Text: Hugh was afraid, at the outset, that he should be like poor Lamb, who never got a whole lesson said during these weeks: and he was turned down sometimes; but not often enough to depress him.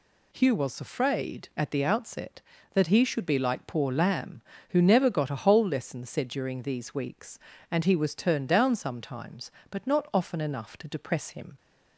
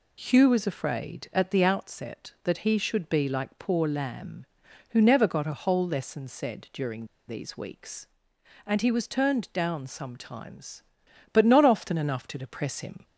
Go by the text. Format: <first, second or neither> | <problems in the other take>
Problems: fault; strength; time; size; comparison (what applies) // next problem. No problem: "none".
first | pauses between "during" and "these"; slight; at 7.0 s; 0.23 s long